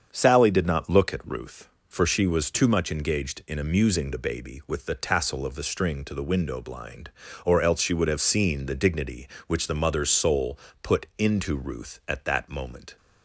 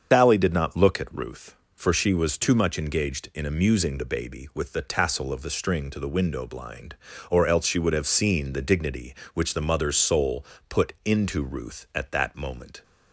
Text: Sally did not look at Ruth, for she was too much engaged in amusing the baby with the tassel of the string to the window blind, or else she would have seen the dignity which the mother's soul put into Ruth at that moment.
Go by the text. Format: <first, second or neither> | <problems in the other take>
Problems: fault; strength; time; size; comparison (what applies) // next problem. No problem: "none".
first | loses the start of "Sally"; at 0.1 s; 125 ms // starts louder than the rest; strong; until 1.1 s; 7 dB; strong in the first // pauses between "soul" and "put"; slight; at 10.4 s; 0.24 s long; slight in the first